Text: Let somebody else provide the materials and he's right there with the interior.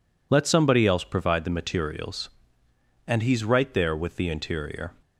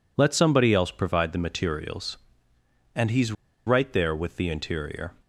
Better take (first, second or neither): first